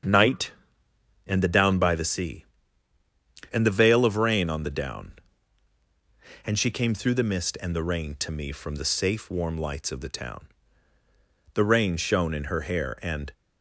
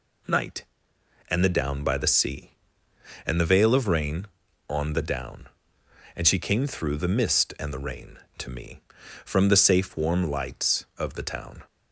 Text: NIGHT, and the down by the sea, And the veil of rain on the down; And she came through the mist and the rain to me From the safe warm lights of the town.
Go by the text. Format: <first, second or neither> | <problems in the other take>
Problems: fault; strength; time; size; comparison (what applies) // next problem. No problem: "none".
second | starts louder than the rest; strong; until 1.7 s; 7.5 dB // goes on to say "The rain shone in her hair And"; strong; from 11.5 s on; 1.7 s long